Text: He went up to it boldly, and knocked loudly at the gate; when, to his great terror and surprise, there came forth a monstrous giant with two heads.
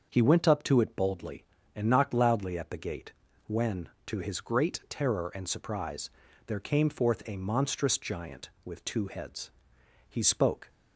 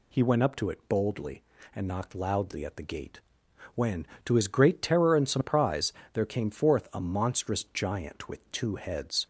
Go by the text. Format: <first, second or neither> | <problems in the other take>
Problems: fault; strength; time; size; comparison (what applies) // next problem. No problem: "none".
second | starts louder than the rest; until 1.1 s; 6.5 dB // goes on to say "He spoke"; noticeable; from 10.0 s on; 0.62 s long